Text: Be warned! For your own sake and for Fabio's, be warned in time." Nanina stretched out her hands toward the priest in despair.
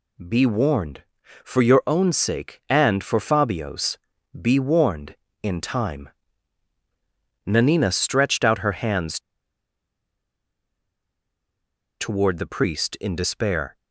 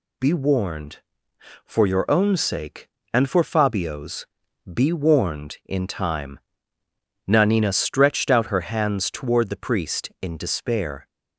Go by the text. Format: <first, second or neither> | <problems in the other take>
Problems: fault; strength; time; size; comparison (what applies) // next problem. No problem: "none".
second | pauses between "hands" and "toward"; strong; at 9.1 s; 2.8 s long